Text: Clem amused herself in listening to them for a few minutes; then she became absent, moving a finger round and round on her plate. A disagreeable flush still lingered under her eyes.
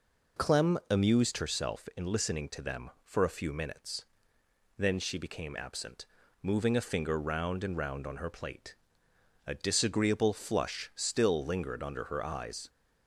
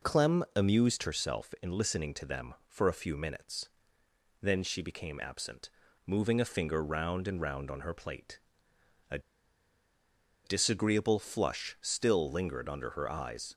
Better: first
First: none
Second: pauses between "A" and "disagreeable"; strong; at 9.1 s; 1.2 s long

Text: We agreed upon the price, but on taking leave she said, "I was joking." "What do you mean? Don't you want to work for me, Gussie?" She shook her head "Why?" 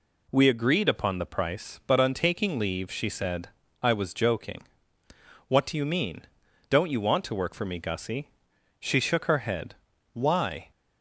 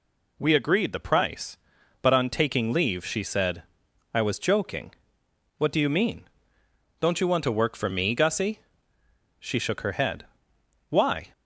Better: first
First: pauses between "head" and "Why"; at 9.7 s; 0.40 s long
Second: skips "upon"; at 0.9 s // pauses between "head" and "Why"; noticeable; at 10.2 s; 0.66 s long

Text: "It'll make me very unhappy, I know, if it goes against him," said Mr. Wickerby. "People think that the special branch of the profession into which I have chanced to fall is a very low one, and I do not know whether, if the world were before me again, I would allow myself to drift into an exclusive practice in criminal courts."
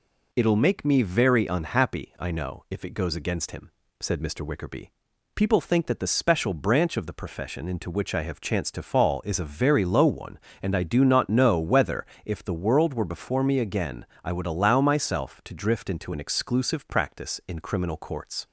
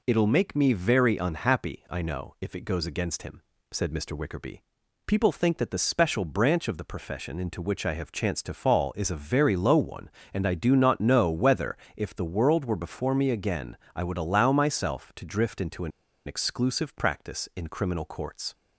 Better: first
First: none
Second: pauses between "an" and "exclusive"; at 15.9 s; 0.36 s long

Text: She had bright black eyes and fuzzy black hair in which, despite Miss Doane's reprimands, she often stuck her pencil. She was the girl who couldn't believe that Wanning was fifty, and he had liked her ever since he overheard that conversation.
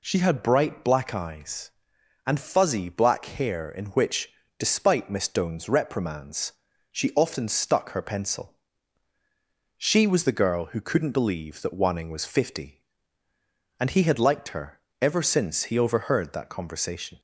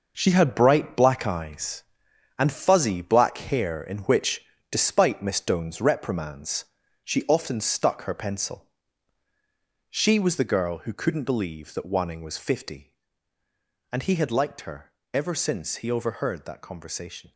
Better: first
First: pauses between "her" and "ever"; slight; at 14.8 s; 0.18 s long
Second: gets quieter; strong; throughout; 9 dB // pauses between "her" and "ever"; slight; at 14.9 s; 0.18 s long

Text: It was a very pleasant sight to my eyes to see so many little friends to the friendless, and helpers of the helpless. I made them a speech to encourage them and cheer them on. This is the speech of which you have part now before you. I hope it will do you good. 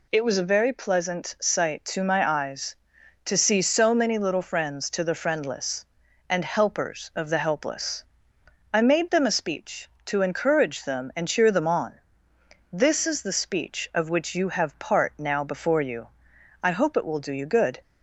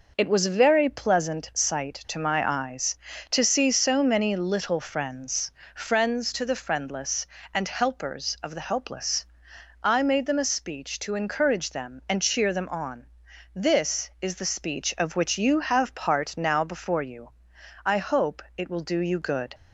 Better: first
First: none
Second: says "friends" twice; at 5.7 s

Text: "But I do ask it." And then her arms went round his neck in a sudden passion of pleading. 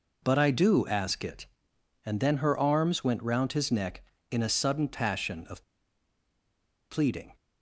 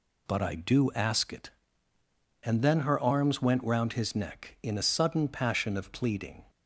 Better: second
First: pauses between "of" and "pleading"; strong; at 5.6 s; 1.2 s long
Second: none

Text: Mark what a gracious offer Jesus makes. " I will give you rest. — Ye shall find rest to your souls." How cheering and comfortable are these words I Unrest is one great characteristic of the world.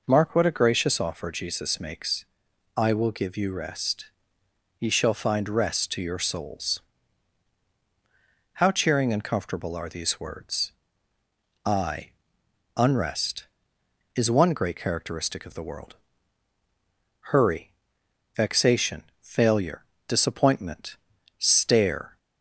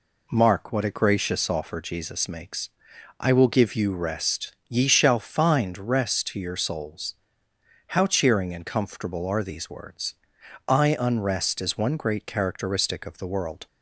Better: second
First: pauses between "words" and "I"; noticeable; at 10.7 s; 0.92 s long // pauses between "I" and "Unrest"; noticeable; at 12.1 s; 0.64 s long // goes on to say "Hurry vexation failure disappointment stare"; strong; from 17.3 s on; 4.8 s long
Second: pauses between "words" and "I"; noticeable; at 10.1 s; 0.52 s long

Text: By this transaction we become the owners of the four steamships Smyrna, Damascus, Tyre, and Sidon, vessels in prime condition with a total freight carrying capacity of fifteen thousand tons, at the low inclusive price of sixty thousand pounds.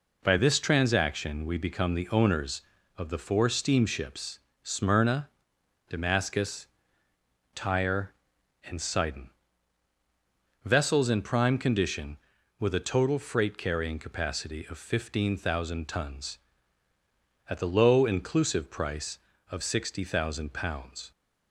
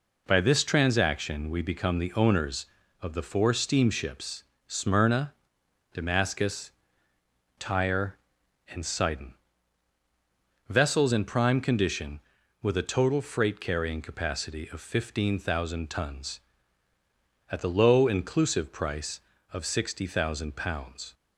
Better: neither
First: pauses between "steamships" and "Smyrna"; slight; at 4.3 s; 0.24 s long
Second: pauses between "steamships" and "Smyrna"; slight; at 4.4 s; 0.24 s long

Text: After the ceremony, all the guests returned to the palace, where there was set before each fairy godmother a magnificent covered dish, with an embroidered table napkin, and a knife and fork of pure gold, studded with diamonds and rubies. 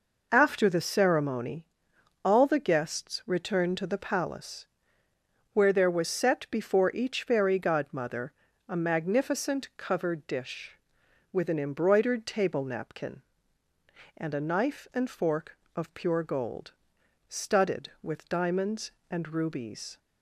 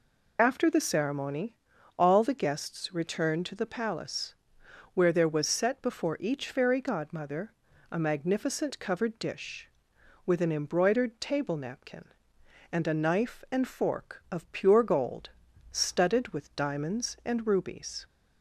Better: first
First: pauses between "godmother" and "a"; slight; at 8.3 s; 0.36 s long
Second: loses the start of "After"; at 0.3 s; 55 ms // pauses between "godmother" and "a"; slight; at 7.5 s; 0.36 s long

